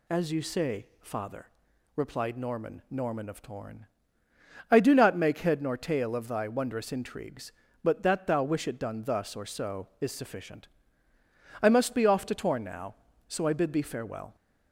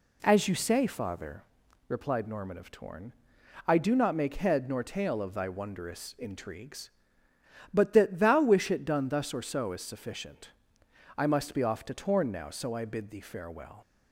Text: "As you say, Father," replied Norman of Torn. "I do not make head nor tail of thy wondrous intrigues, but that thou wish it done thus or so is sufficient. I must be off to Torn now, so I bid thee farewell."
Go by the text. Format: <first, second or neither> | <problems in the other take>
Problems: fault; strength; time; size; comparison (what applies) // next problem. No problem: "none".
second | says "Norman" twice; at 2.9 s